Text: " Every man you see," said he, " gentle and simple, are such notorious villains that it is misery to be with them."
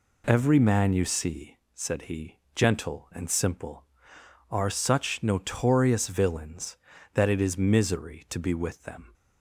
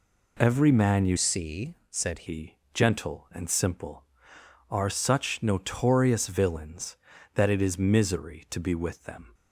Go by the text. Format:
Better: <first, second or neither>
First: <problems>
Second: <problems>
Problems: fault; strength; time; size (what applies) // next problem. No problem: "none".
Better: first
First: none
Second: changes voice from "see" to "said"; from 1.1 to 2.2 s; 1.1 s long